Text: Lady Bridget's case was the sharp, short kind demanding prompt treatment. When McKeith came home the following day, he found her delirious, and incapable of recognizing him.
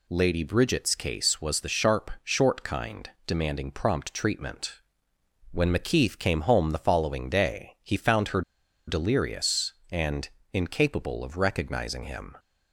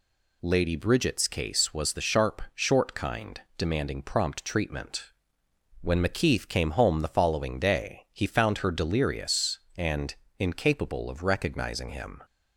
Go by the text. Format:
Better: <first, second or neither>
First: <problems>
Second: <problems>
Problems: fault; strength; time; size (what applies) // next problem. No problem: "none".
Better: second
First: pauses between "kind" and "demanding"; slight; at 3.0 s; 0.18 s long // pauses between "her" and "delirious"; noticeable; at 8.4 s; 0.46 s long // pauses between "and" and "incapable"; slight; at 10.2 s; 0.24 s long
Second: pauses between "kind" and "demanding"; slight; at 3.4 s; 0.18 s long // pauses between "and" and "incapable"; slight; at 10.1 s; 0.24 s long